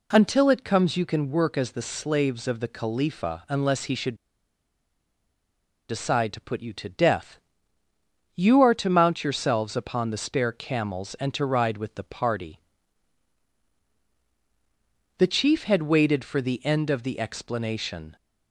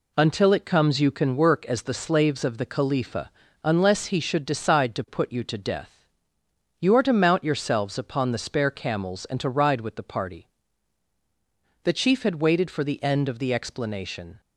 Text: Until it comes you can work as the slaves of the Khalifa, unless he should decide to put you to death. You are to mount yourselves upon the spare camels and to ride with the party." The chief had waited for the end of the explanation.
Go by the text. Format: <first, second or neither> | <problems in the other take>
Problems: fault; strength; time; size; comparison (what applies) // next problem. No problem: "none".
second | pauses between "should" and "decide"; strong; at 4.1 s; 1.7 s long